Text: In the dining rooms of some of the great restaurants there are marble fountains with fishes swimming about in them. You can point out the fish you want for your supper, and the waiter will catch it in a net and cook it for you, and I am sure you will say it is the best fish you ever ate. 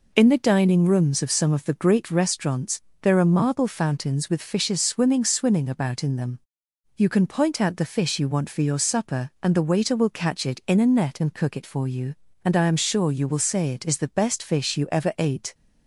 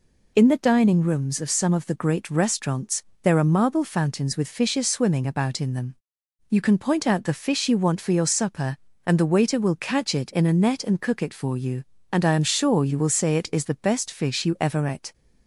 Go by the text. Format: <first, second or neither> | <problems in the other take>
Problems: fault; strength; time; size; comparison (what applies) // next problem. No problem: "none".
second | pauses between "restaurants" and "there"; slight; at 2.8 s; 0.18 s long; slight in the second // says "swimming" twice; at 5.2 s